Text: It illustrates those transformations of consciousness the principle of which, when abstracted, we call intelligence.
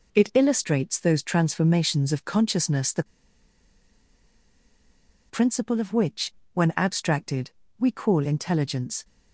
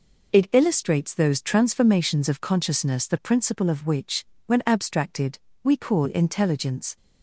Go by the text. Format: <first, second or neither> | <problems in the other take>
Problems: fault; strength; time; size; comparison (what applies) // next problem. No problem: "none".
second | pauses between "the" and "principle"; strong; at 3.0 s; 2.2 s long